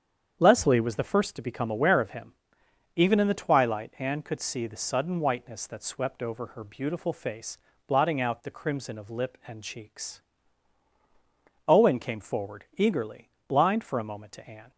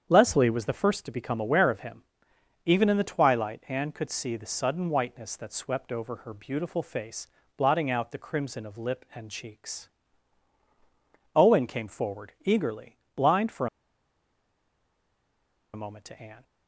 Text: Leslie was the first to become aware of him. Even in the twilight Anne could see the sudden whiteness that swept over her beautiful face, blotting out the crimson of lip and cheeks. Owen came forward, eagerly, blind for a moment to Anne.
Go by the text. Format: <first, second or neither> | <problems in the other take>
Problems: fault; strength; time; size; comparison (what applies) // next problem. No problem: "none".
first | starts louder than the rest; strong; until 1.1 s; 8 dB; strong in the first // pauses between "for" and "a"; strong; at 13.6 s; 2.0 s long